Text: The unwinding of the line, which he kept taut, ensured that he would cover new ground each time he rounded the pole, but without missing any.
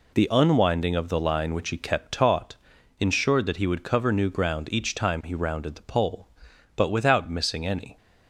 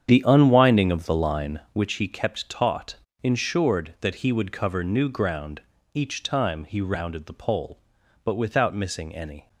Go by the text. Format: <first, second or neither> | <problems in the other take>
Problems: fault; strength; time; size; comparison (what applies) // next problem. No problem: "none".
first | starts louder than the rest; strong; until 1.9 s; 8.5 dB // pauses between "ground" and "each"; slight; at 5.5 s; 0.34 s long